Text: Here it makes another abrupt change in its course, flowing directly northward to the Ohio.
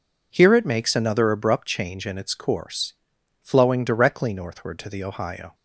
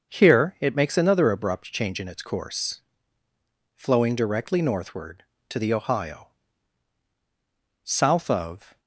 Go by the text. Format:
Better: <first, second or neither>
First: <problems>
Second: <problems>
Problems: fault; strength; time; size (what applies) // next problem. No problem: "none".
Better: first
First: none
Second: starts louder than the rest; until 1.1 s; 6.5 dB // goes on to say "South of"; noticeable; from 7.8 s on; 0.96 s long